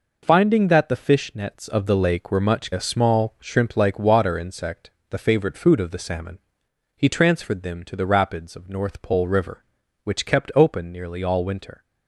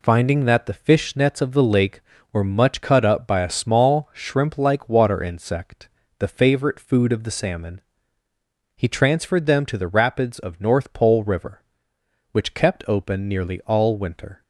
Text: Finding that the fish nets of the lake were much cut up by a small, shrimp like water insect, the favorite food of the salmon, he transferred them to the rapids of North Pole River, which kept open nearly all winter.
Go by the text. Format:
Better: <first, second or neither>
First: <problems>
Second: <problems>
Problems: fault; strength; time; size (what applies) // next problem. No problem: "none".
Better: second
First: skips "cut up by"; at 2.7 s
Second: none